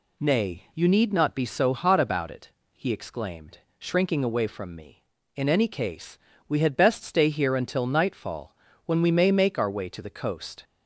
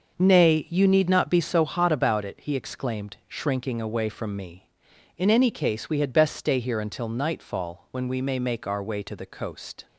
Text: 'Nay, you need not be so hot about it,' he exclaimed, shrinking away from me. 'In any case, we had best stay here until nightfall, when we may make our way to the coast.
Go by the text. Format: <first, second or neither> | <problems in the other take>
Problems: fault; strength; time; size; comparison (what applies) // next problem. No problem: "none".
first | starts louder than the rest; until 1.6 s; 6 dB